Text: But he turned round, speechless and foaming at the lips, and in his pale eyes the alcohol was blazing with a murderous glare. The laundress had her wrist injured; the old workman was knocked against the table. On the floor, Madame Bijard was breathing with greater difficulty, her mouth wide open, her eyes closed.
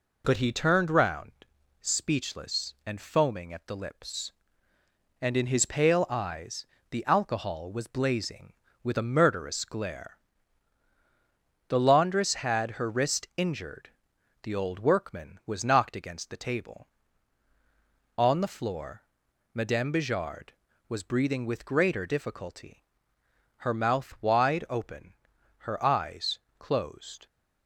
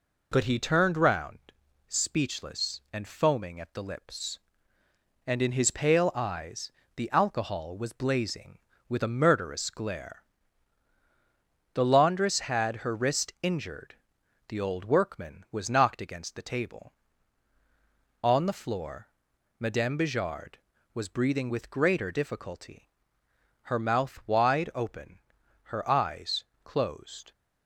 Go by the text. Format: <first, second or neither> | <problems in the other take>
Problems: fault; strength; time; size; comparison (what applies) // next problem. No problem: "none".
neither | pauses between "eyes" and "the"; slight; the same in both // pauses between "eyes" and "closed"; slight; the same in both